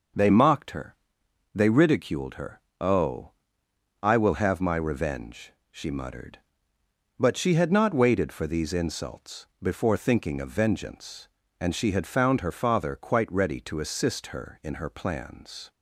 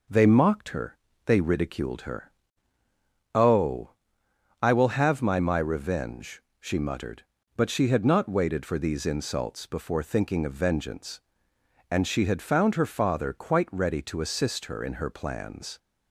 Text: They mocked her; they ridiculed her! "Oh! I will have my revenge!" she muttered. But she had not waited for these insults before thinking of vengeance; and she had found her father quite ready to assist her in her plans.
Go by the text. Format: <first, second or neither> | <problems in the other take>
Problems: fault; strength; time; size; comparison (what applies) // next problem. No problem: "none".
first | says "my" twice; at 5.3 s